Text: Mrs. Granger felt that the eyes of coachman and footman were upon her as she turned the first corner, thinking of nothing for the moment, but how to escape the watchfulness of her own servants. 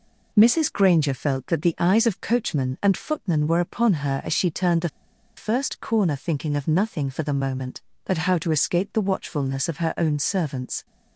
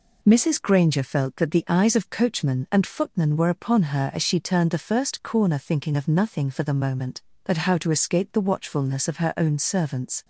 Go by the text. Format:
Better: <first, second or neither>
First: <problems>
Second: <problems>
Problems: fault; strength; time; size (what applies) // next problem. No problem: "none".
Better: second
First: pauses between "the" and "first"; noticeable; at 4.8 s; 0.48 s long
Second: none